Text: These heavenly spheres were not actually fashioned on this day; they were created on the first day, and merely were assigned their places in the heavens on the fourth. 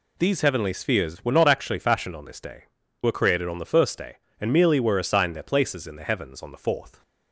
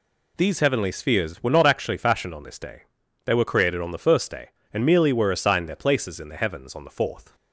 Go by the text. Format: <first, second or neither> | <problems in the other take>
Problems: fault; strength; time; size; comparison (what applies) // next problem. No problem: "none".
second | skips "they"; at 2.8 s